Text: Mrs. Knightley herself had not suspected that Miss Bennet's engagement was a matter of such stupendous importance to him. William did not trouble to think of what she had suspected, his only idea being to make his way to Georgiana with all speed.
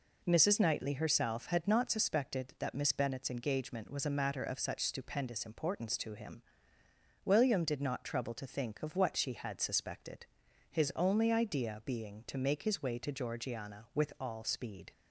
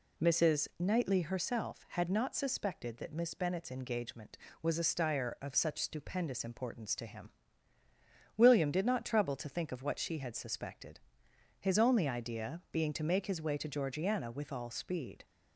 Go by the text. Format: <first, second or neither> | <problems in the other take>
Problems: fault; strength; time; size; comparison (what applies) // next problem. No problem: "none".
first | says "stire" for "matter"; at 4.8 s